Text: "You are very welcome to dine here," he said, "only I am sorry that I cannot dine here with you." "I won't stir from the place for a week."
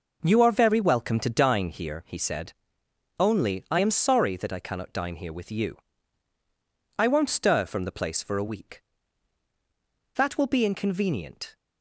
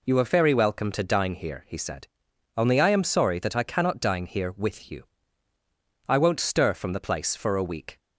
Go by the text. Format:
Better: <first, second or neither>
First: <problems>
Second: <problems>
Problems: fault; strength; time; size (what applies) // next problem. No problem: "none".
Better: second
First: goes on to say "That will be inconvenient"; from 10.1 s on; 1.4 s long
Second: none